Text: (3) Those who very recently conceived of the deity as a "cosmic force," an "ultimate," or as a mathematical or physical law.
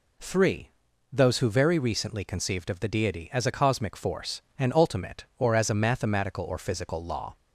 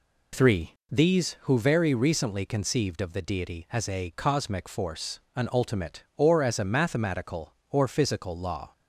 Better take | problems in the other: first | says "These" for "Those"; at 0.9 s

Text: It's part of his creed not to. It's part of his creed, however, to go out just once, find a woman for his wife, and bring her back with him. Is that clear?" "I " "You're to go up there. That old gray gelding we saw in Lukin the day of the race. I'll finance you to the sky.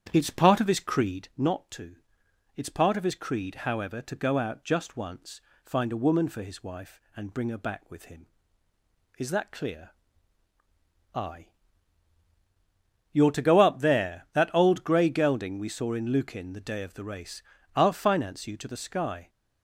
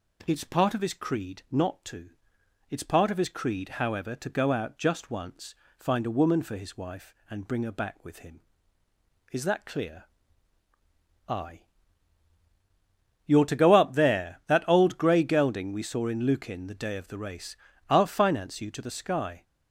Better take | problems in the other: second | starts louder than the rest; strong; until 1.3 s; 9 dB

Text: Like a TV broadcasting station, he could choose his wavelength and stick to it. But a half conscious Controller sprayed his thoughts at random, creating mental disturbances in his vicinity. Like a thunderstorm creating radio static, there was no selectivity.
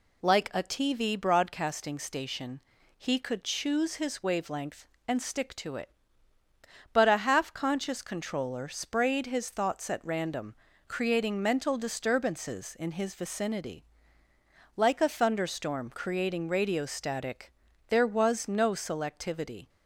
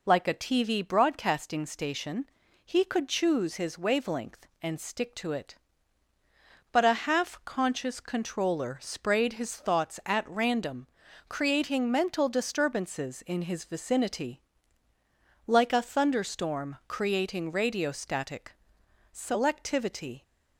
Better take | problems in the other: first | skips "there was no"; at 18.8 s

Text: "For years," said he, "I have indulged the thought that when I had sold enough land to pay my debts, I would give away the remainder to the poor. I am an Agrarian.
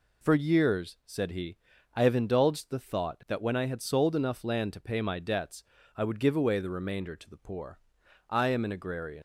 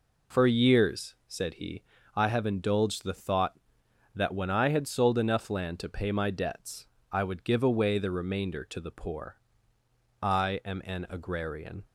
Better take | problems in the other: second | leaves "Agrarian" unfinished; at 9.1 s; 120 ms

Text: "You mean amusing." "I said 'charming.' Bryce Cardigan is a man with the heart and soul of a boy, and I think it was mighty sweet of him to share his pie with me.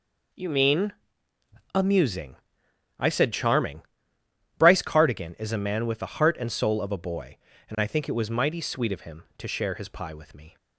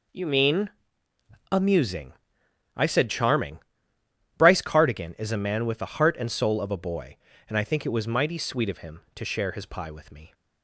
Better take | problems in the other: neither | pauses between "mean" and "amusing"; noticeable; the same in both

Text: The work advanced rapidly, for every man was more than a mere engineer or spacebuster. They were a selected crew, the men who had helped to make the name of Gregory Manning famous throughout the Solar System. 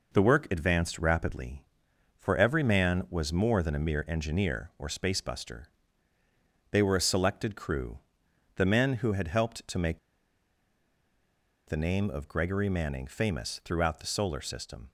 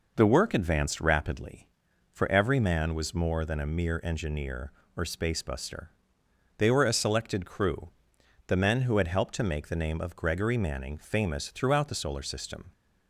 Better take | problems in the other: second | pauses between "make" and "the"; strong; at 9.9 s; 1.6 s long

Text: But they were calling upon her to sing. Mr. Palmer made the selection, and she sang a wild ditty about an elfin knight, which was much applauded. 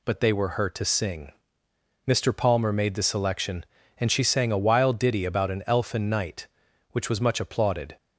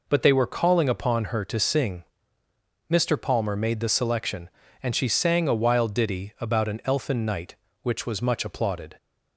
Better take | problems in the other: second | skips "calling upon"; at 0.5 s

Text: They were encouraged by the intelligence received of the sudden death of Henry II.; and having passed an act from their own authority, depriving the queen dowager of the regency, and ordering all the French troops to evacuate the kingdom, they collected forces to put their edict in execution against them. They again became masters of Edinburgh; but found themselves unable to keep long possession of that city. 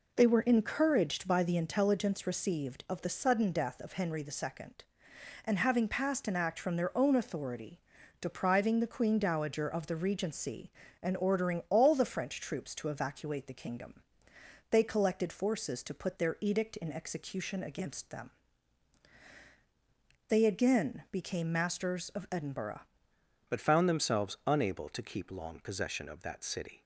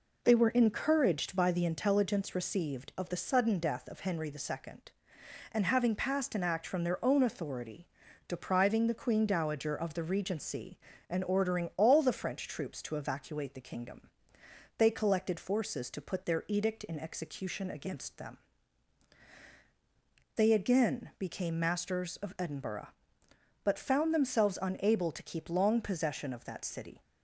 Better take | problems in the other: second | changes voice at "but"; from 23.4 s on; 3.4 s long

